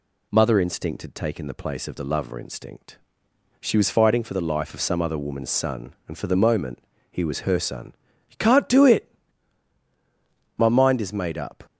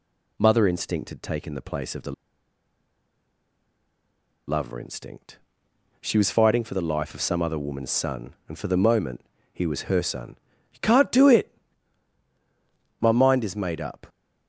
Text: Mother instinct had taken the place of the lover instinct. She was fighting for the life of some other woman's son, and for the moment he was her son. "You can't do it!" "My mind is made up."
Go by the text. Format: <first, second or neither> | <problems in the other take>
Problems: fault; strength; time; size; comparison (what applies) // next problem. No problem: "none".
first | pauses between "the" and "lover"; strong; at 2.1 s; 2.3 s long // pauses between "moment" and "he"; slight; at 9.2 s; 0.32 s long; slight in the first